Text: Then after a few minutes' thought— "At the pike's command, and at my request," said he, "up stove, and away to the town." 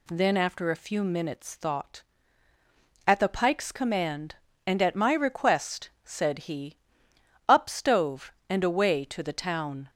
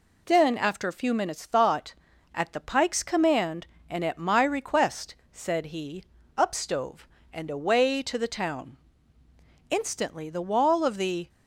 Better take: first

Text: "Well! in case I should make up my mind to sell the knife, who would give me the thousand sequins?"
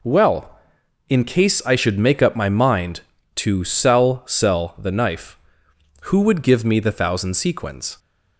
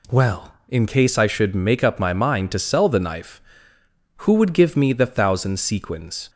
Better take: second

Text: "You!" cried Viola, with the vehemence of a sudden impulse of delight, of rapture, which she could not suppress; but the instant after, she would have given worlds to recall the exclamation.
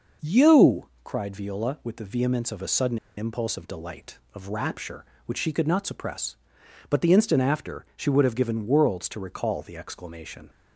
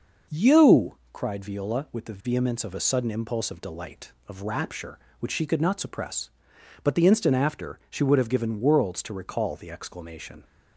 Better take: second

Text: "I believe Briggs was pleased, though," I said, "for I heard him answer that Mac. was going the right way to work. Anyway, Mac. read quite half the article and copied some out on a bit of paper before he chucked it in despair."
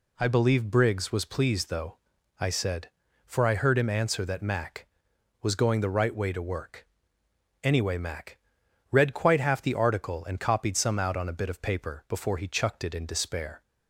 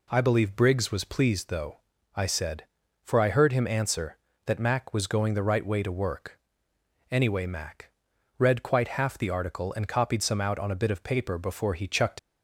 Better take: first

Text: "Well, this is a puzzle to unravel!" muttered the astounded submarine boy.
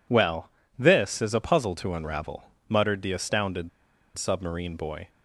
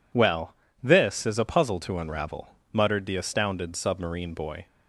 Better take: second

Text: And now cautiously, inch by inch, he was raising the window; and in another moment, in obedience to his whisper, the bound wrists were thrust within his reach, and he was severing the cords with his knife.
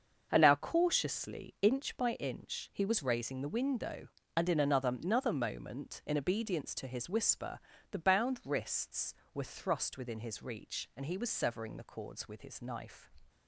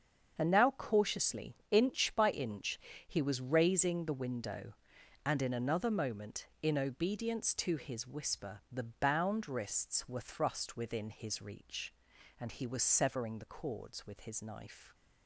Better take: second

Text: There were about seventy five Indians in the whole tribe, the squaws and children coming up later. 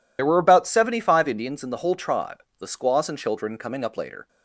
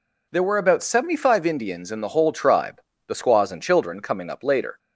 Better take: second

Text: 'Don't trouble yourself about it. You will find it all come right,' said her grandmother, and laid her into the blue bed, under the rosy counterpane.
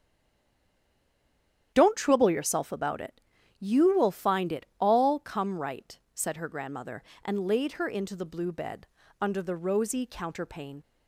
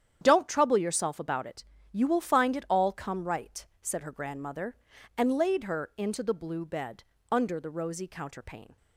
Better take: second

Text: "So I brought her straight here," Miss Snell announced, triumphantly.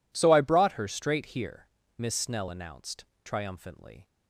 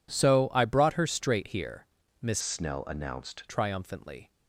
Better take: first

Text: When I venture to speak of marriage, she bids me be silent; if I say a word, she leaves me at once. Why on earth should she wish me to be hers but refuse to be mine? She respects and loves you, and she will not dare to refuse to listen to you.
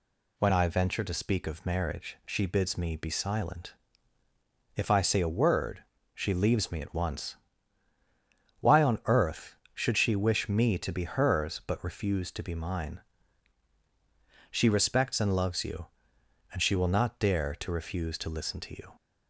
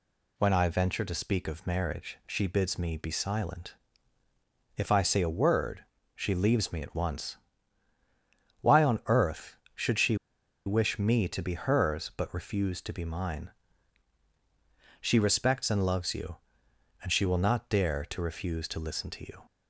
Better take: first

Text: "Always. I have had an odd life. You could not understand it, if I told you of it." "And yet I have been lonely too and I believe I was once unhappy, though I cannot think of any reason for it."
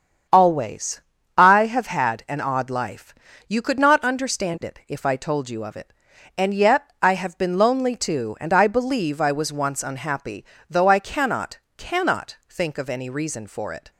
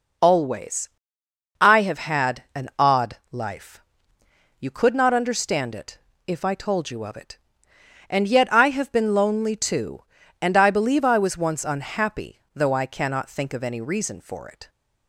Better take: second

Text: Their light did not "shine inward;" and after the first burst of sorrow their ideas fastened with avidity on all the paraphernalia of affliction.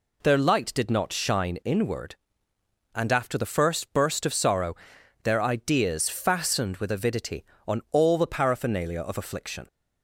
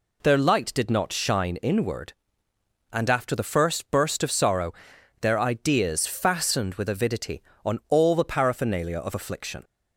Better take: neither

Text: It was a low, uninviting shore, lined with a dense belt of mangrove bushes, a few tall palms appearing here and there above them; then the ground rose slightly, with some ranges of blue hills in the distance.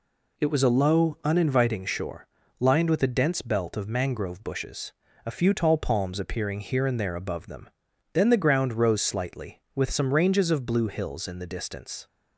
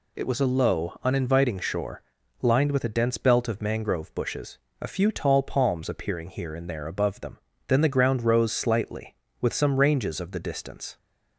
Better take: first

